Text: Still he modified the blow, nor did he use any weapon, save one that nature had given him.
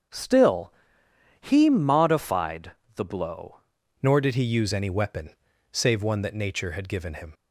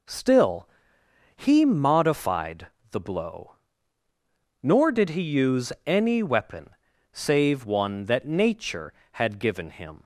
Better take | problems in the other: second | starts louder than the rest; until 1.7 s; 7 dB // pauses between "Still" and "he"; noticeable; at 0.7 s; 0.68 s long; noticeable in the second // pauses between "modified" and "the"; slight; at 2.7 s; 0.22 s long; slight in the second // changes voice at "nor"; from 4.0 s on; 3.3 s long

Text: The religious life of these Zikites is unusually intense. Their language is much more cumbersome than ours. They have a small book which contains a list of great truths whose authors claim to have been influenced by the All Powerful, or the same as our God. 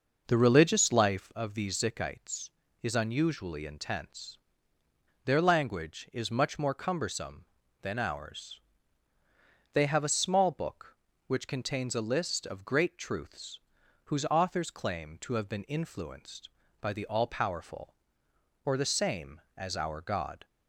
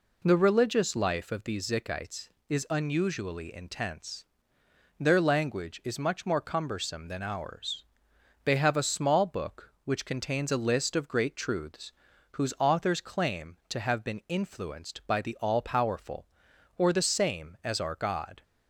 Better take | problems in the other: second | starts louder than the rest; noticeable; until 1.5 s; 5.5 dB // pauses between "truths" and "whose"; noticeable; at 13.5 s; 0.46 s long; also in the second

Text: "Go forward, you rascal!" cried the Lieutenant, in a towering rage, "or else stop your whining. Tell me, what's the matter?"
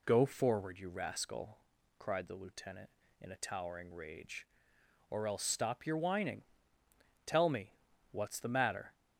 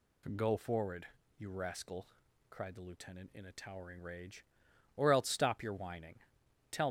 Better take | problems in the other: first | stops before "me what's the matter"; at 6.8 s

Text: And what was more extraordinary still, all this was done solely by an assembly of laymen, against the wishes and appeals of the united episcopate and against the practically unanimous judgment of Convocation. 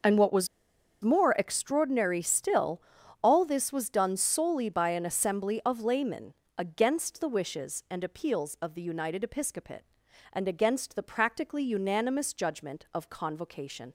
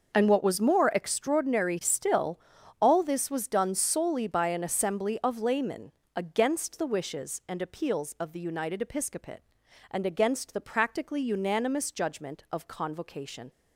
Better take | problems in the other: second | starts louder than the rest; until 1.6 s; 6.5 dB; also in the second // pauses between "was" and "more"; noticeable; at 0.4 s; 0.56 s long

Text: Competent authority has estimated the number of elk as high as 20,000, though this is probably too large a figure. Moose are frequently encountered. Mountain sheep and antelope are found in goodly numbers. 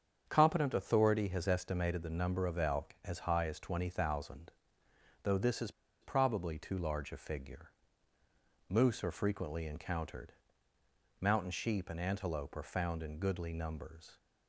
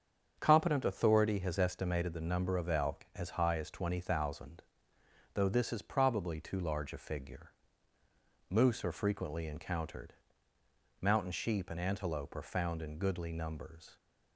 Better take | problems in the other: second | starts louder than the rest; strong; until 1.2 s; 7.5 dB; strong in the second // pauses between "is" and "probably"; slight; at 5.7 s; 0.31 s long

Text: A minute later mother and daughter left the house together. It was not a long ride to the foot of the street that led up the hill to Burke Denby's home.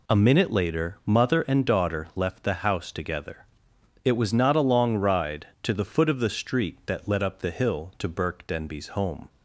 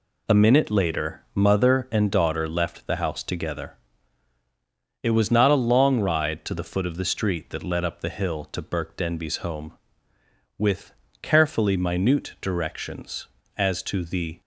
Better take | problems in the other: first | goes on to say "With carefully minute directions as to the"; strong; from 10.5 s on; 3.8 s long

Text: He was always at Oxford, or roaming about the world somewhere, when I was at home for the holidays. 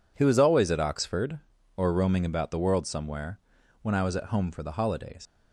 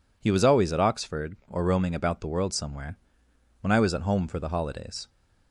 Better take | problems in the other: second | leaves "holidays" unfinished; at 5.2 s; 95 ms

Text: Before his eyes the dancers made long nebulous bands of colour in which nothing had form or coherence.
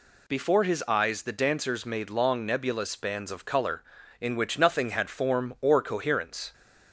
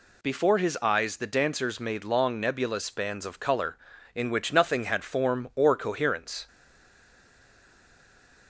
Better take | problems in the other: first | stays silent after the last word; noticeable; from 6.4 s on; 2.0 s long

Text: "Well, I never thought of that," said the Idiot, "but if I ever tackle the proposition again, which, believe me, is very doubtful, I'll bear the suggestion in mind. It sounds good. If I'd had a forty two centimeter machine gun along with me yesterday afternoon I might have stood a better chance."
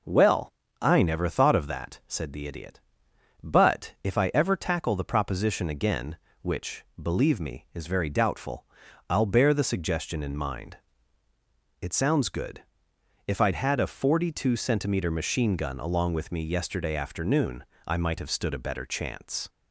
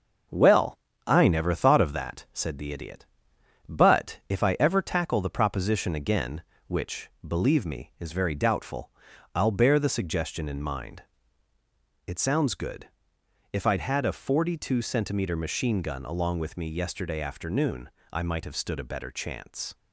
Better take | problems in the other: first | gets quieter; noticeable; throughout; 4 dB // pauses between "afternoon" and "I"; slight; at 17.8 s; 0.24 s long; slight in the first

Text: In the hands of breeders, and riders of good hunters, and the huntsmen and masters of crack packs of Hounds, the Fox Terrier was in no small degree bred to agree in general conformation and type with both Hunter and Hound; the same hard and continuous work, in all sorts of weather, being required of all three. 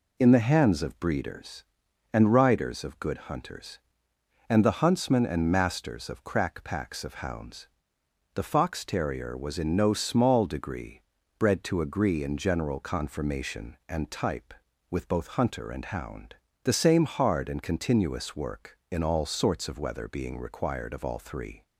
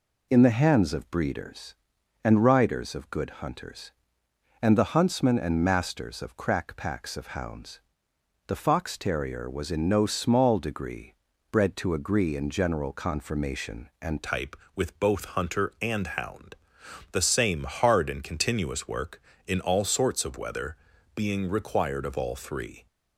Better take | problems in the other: first | pauses between "degree" and "bred"; slight; at 11.1 s; 0.36 s long; slight in the first // changes voice at "type"; from 14.2 s on; 8.6 s long

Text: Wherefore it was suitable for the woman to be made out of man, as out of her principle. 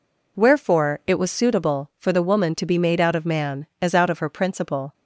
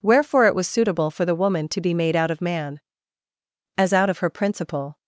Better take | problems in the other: neither | none

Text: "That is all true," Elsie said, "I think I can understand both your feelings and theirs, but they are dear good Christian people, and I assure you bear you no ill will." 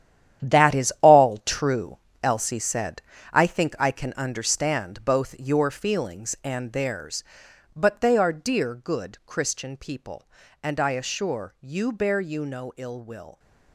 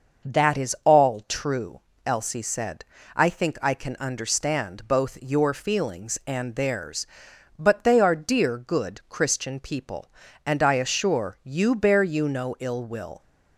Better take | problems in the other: second | gets quieter; strong; throughout; 11 dB // starts louder than the rest; strong; until 1.6 s; 10.5 dB; noticeable in the second

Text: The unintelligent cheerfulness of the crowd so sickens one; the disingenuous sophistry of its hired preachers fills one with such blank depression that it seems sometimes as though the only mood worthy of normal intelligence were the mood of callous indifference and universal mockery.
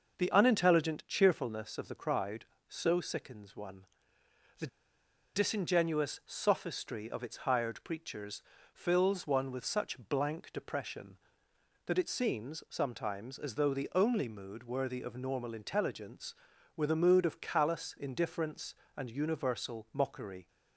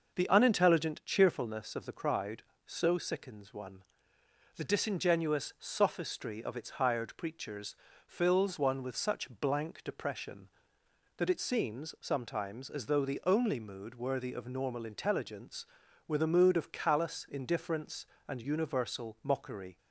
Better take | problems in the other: second | pauses between "the" and "disingenuous"; noticeable; at 4.6 s; 0.67 s long // pauses between "preachers" and "fills"; slight; at 8.4 s; 0.32 s long; slight in the second

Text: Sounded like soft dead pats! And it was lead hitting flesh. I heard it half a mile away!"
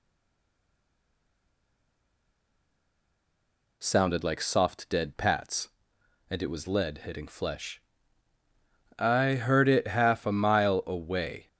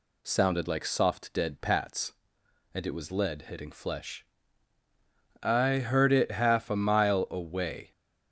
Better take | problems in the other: second | stays silent before the first word; strong; until 3.7 s; 3.7 s long

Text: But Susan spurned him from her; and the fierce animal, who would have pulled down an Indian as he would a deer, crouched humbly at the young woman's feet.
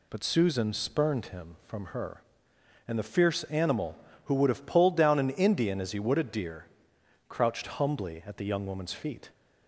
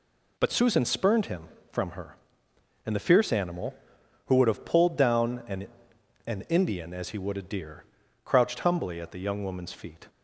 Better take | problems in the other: first | says "an" twice; at 6.2 s

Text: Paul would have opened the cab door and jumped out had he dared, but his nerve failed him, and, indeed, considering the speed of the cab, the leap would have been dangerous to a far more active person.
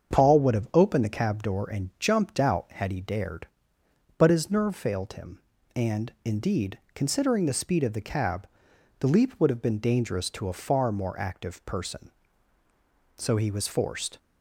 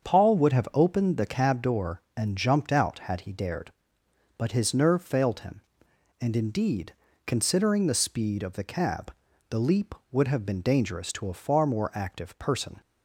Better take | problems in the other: second | starts louder than the rest; until 1.1 s; 7 dB; also in the second // goes on to say "So he was forced"; noticeable; from 13.1 s on; 1.0 s long

